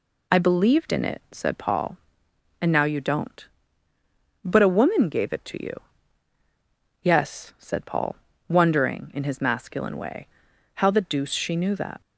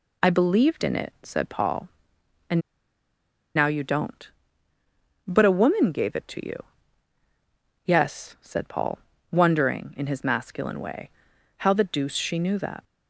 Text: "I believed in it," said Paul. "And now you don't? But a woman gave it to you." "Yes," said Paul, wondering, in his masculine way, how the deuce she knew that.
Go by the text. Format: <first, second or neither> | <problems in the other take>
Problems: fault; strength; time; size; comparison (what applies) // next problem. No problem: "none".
first | pauses between "And" and "now"; noticeable; at 2.5 s; 0.96 s long